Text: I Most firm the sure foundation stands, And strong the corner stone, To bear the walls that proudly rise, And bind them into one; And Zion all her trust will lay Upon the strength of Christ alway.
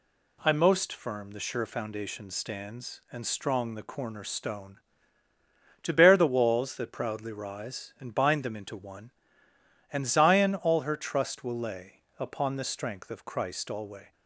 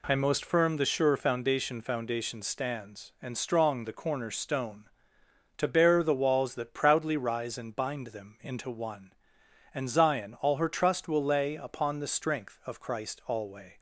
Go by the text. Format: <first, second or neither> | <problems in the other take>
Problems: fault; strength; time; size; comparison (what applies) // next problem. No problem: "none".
first | says "foundation" twice; at 1.8 s